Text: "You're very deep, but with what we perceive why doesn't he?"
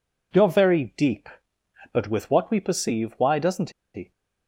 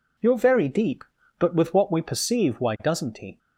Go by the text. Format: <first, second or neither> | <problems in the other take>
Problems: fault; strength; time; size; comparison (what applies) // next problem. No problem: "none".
second | pauses between "doesn't" and "he"; slight; at 3.7 s; 0.23 s long